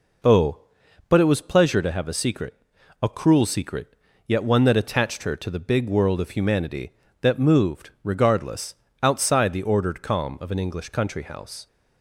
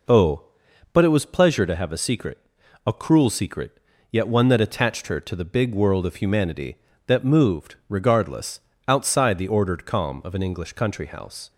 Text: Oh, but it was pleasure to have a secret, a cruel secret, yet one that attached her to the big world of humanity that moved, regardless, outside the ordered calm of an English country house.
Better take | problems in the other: neither | none

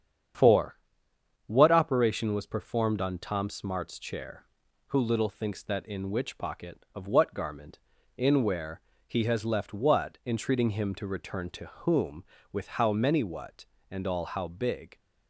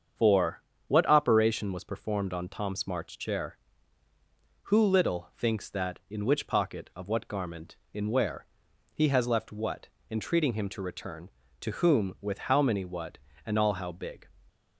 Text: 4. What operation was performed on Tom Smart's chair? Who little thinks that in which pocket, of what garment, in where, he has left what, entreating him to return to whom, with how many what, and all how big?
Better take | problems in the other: neither | starts louder than the rest; strong; the same in both

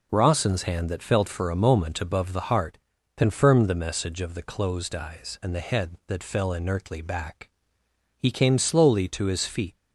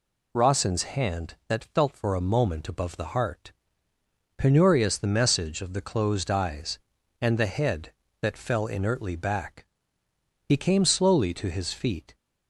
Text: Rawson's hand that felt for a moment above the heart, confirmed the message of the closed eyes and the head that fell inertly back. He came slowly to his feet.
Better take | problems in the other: first | says "penurious" for "confirmed"; at 4.3 s

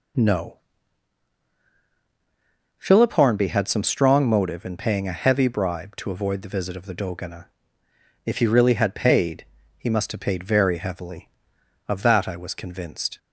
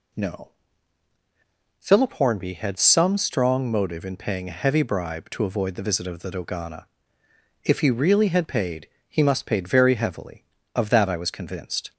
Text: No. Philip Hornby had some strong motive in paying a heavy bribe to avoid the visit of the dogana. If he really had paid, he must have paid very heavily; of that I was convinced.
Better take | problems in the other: first | skips "have"; at 9.4 s

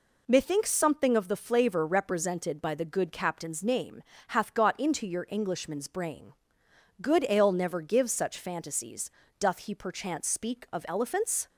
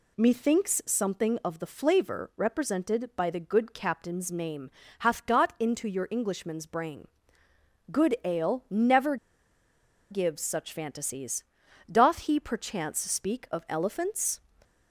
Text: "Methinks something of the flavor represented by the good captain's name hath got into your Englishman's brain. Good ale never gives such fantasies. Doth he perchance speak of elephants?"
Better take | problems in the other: first | pauses between "name" and "hath"; slight; at 4.6 s; 0.30 s long; slight in the first // pauses between "never" and "gives"; noticeable; at 9.1 s; 0.94 s long

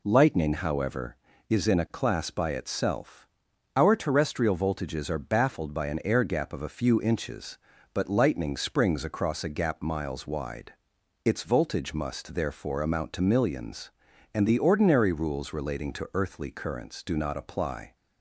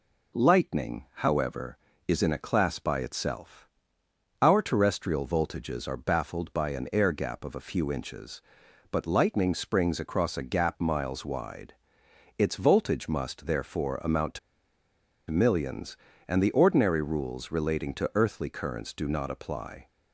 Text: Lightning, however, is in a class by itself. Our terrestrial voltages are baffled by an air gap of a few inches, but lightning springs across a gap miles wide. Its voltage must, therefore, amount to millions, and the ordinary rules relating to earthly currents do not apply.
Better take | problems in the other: first | pauses between "to" and "millions"; noticeable; at 14.3 s; 0.91 s long

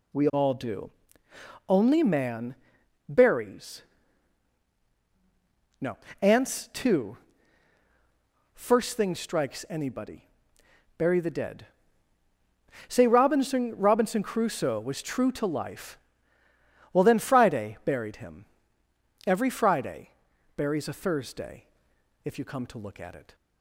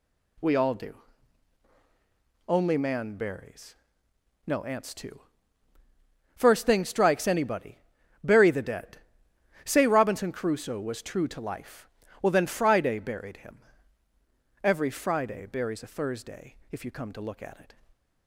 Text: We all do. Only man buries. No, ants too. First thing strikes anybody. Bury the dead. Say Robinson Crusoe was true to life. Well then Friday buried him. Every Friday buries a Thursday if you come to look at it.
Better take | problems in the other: second | pauses between "man" and "buries"; noticeable; at 2.5 s; 0.54 s long // says "Robinson" twice; at 13.7 s // pauses between "Friday" and "buries"; noticeable; at 20.1 s; 0.46 s long // pauses between "Thursday" and "if"; noticeable; at 21.6 s; 0.58 s long; slight in the second

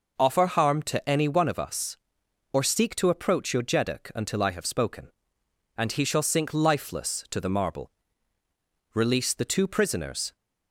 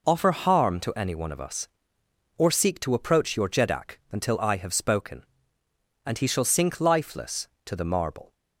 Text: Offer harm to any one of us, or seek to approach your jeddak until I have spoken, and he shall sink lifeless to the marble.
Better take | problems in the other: second | goes on to say "Release the two prisoners"; from 8.9 s on; 1.4 s long

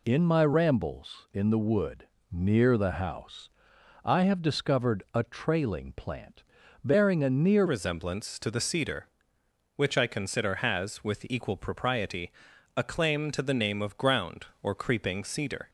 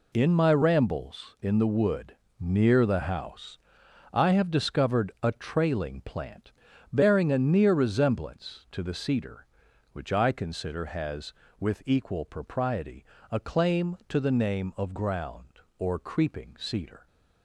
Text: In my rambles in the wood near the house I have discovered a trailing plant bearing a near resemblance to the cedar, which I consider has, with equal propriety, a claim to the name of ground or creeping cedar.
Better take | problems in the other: second | pauses between "wood" and "near"; slight; at 2.0 s; 0.24 s long; slight in the second // pauses between "house" and "I"; noticeable; at 3.4 s; 0.56 s long; noticeable in the second // pauses between "plant" and "bearing"; at 6.4 s; 0.40 s long; also in the second // changes voice at "resemblance"; from 7.6 s on; 8.0 s long

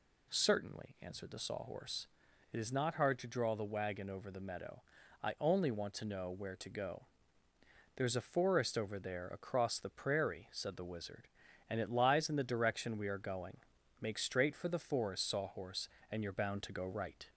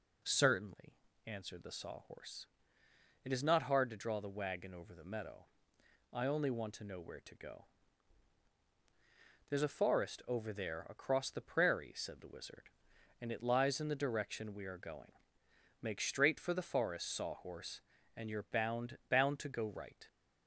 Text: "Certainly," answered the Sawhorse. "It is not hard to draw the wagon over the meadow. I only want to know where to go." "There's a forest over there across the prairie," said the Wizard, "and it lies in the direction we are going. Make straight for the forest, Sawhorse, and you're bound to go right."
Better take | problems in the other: first | says "bound" twice; at 19.0 s

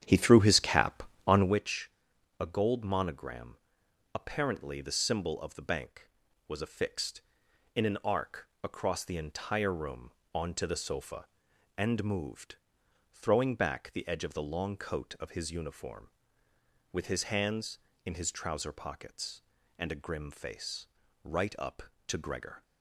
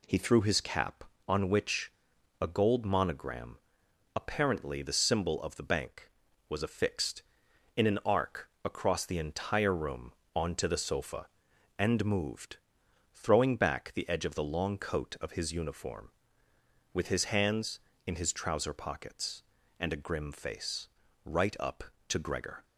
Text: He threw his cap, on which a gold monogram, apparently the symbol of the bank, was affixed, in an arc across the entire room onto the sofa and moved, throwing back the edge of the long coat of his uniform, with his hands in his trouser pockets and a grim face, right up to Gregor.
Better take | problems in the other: second | starts louder than the rest; strong; until 1.6 s; 9.5 dB // pauses between "which" and "a"; noticeable; at 1.9 s; 0.48 s long; noticeable in the second // pauses between "arc" and "across"; slight; at 8.4 s; 0.16 s long; slight in the second // pauses between "room" and "onto"; slight; at 10.1 s; 0.22 s long; slight in the second

